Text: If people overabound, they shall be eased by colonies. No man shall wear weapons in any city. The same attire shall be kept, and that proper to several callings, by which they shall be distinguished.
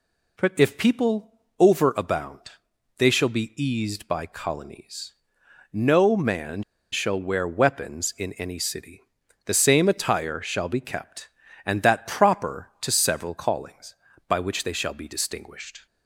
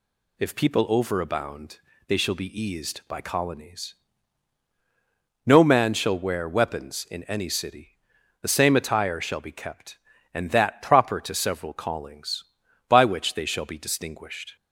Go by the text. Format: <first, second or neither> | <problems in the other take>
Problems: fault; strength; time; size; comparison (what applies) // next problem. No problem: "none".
second | pauses between "people" and "overabound"; slight; at 1.3 s; 0.26 s long // pauses between "man" and "shall"; slight; at 6.6 s; 0.30 s long